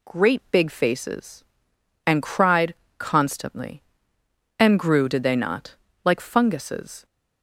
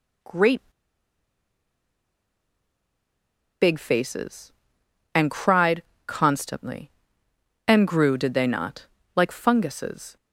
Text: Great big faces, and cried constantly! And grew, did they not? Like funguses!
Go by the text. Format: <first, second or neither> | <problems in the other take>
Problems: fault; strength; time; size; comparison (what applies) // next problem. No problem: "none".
first | pauses between "Great" and "big"; strong; at 0.6 s; 3.0 s long // pauses between "cried" and "constantly"; slight; at 5.8 s; 0.24 s long; slight in the first